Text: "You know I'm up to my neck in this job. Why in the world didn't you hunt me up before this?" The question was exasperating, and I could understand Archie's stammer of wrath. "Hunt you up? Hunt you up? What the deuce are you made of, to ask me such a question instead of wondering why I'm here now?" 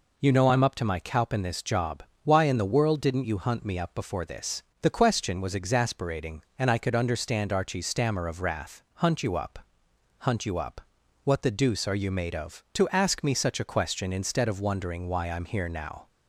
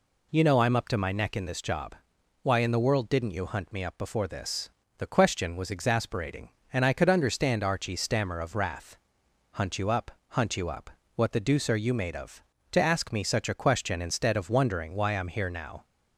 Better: second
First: says "cowp" for "neck"; at 0.9 s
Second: none

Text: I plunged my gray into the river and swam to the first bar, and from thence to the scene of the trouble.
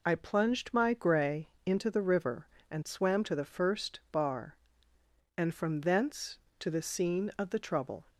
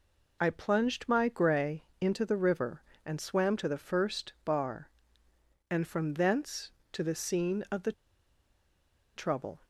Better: first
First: pauses between "gray" and "into"; slight; at 1.4 s; 0.16 s long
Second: pauses between "gray" and "into"; slight; at 1.8 s; 0.16 s long // pauses between "the" and "trouble"; at 7.9 s; 1.2 s long

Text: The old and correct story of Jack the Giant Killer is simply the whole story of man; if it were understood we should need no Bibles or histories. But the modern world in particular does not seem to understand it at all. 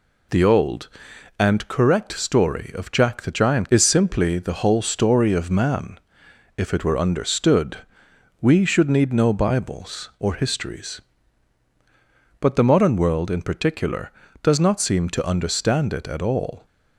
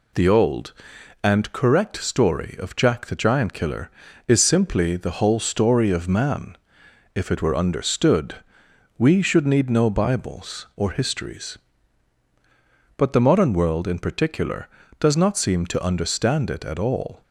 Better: second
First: skips "Killer"; at 3.6 s // pauses between "understood" and "we"; noticeable; at 7.7 s; 0.64 s long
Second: pauses between "understood" and "we"; noticeable; at 8.3 s; 0.63 s long

